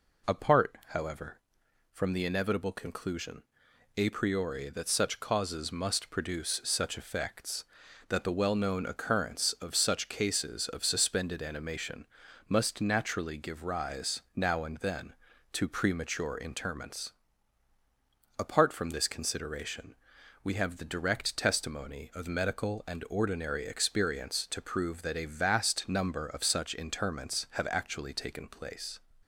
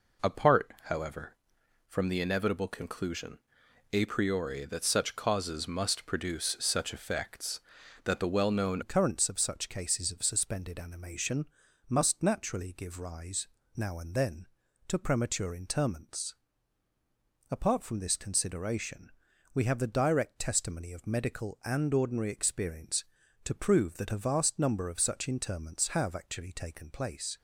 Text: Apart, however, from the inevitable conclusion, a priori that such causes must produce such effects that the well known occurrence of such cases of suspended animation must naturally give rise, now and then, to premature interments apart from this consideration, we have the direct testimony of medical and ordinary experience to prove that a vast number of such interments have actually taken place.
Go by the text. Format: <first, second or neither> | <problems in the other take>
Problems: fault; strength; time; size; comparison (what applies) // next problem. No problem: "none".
first | changes voice at "occurrence"; from 8.8 s on; 18.5 s long // pauses between "animation" and "must"; at 11.4 s; 0.40 s long; also in the first // pauses between "interments" and "apart"; at 16.3 s; 1.1 s long; also in the first